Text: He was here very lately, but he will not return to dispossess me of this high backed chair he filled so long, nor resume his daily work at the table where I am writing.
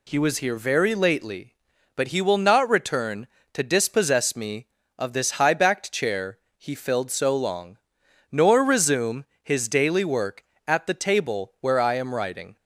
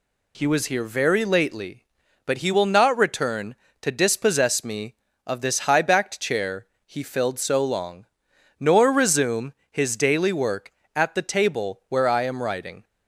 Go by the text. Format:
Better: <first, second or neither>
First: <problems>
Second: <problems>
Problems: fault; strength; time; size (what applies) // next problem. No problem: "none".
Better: neither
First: pauses between "chair" and "he"; slight; at 6.3 s; 0.18 s long // pauses between "resume" and "his"; slight; at 9.2 s; 0.18 s long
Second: pauses between "chair" and "he"; slight; at 6.6 s; 0.18 s long // pauses between "resume" and "his"; slight; at 9.5 s; 0.18 s long